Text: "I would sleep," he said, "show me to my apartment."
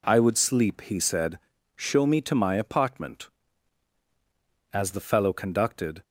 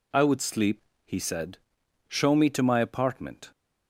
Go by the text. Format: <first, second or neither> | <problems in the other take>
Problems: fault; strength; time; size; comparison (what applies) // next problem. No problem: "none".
second | goes on to say "As the fellow conducted"; from 4.7 s on; 1.3 s long